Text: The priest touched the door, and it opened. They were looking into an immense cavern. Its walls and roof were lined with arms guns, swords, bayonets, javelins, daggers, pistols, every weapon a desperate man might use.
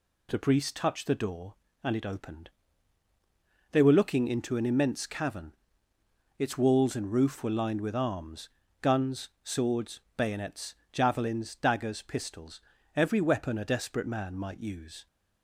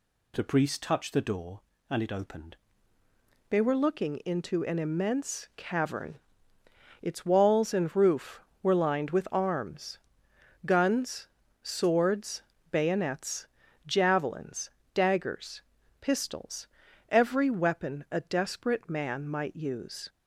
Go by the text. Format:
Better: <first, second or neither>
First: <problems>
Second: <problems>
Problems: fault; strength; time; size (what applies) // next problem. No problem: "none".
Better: first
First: pauses between "arms" and "guns"; slight; at 8.4 s; 0.32 s long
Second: changes voice at "They"; from 3.5 s on; 16.5 s long // pauses between "arms" and "guns"; noticeable; at 9.9 s; 0.66 s long